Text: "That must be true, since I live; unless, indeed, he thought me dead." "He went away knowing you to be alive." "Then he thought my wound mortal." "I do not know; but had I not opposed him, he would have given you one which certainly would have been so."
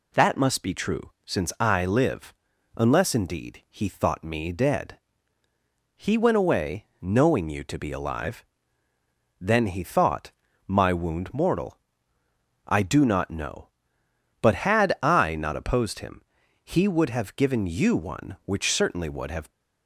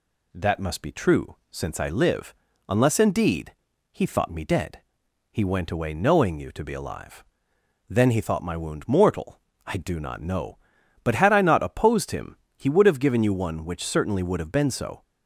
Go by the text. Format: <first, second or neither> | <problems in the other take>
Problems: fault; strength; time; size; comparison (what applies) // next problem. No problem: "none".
second | pauses between "thought" and "my"; slight; at 10.3 s; 0.34 s long // stops before "been so"; at 19.5 s